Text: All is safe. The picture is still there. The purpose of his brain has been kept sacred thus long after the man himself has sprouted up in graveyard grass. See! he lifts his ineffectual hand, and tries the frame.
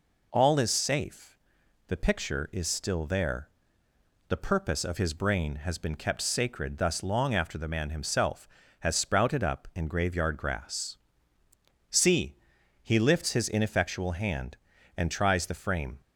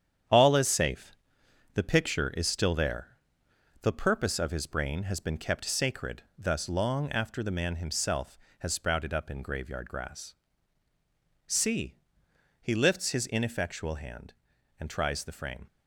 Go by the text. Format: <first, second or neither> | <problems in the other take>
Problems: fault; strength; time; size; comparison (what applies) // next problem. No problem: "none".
first | gets quieter; throughout; 7 dB